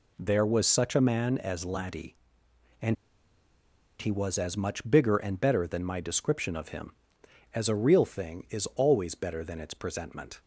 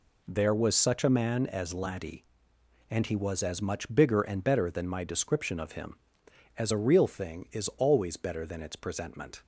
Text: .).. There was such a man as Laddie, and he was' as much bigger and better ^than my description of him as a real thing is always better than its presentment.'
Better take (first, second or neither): second